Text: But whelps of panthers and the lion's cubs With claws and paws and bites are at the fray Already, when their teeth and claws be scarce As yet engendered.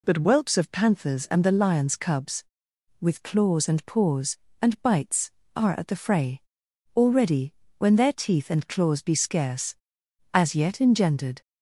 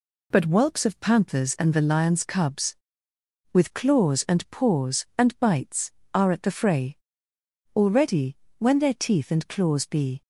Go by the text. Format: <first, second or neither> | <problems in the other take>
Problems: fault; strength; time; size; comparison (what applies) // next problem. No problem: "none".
first | pauses between "fray" and "Already"; noticeable; at 6.9 s; 0.80 s long; noticeable in the first // stops before "scarce As yet engendered"; at 10.2 s